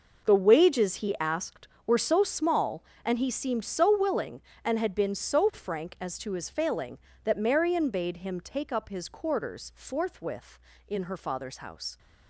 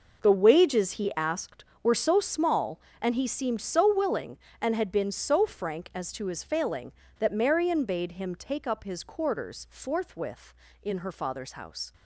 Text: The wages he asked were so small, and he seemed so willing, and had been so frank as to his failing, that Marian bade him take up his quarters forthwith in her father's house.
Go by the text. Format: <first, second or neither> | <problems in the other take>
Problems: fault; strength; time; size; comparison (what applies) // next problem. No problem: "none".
neither | none